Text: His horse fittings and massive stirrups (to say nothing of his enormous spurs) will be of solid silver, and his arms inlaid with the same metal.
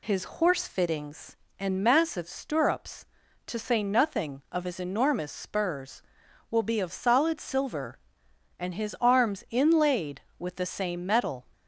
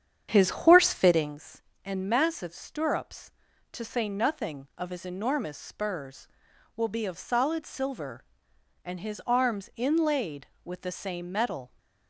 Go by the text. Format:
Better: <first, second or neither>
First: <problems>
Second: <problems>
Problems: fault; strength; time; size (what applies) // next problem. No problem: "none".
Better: first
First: none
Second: starts louder than the rest; strong; until 1.4 s; 8 dB